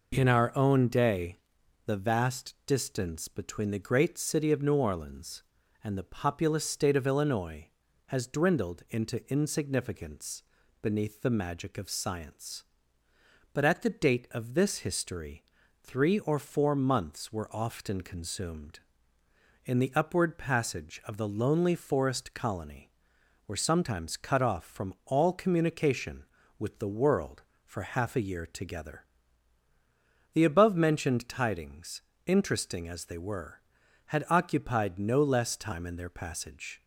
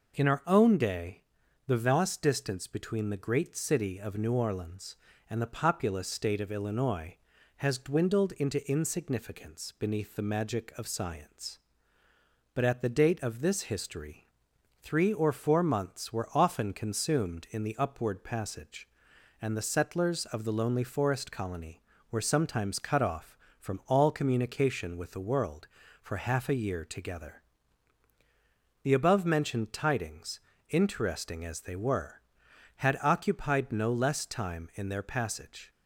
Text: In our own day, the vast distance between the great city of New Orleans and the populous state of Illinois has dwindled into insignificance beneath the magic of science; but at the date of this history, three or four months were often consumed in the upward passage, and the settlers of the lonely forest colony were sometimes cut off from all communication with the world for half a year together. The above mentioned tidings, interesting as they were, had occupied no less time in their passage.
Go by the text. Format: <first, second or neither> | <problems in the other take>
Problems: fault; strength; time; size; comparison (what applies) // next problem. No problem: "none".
second | pauses between "insignificance" and "beneath"; at 10.4 s; 0.38 s long // skips "and the settlers"; at 21.0 s